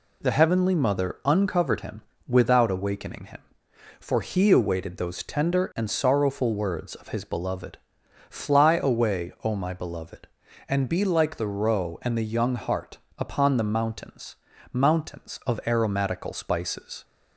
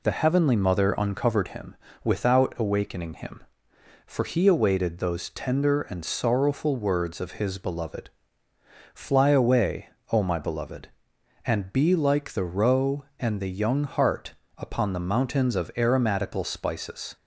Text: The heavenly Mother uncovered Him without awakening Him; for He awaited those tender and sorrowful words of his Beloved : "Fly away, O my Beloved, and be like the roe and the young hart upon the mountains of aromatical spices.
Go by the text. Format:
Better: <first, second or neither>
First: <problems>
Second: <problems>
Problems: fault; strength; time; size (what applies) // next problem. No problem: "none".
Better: second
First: pauses between "Him" and "without"; slight; at 2.0 s; 0.26 s long // pauses between "hart" and "upon"; slight; at 12.9 s; 0.18 s long // says "mountains" twice; at 14.7 s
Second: pauses between "Him" and "without"; slight; at 1.7 s; 0.28 s long // pauses between "hart" and "upon"; slight; at 14.3 s; 0.22 s long